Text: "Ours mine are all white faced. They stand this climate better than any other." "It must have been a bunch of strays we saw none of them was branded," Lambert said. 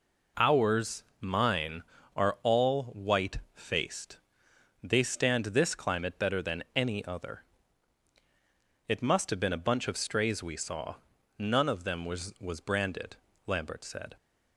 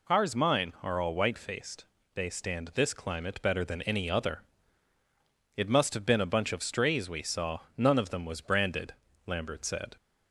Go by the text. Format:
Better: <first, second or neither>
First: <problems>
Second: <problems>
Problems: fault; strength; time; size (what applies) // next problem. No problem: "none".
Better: second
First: pauses between "Ours" and "mine"; slight; at 1.0 s; 0.16 s long // pauses between "saw" and "none"; at 10.9 s; 0.42 s long // says "was" twice; at 12.3 s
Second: none